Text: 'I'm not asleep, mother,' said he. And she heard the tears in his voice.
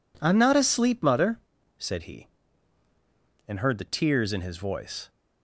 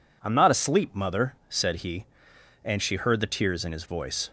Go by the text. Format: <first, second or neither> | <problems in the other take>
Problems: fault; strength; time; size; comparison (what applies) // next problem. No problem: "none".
second | skips "she"; at 3.5 s